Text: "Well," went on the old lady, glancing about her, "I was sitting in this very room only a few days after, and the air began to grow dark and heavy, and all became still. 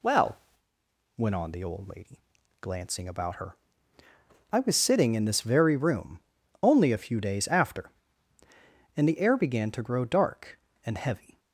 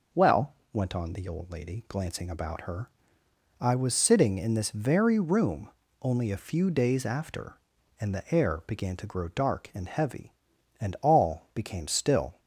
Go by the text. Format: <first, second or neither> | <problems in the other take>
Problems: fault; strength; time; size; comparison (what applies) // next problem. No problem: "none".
second | pauses between "room" and "only"; at 6.1 s; 0.42 s long; slight in the second // stops before "and all became still"; at 11.3 s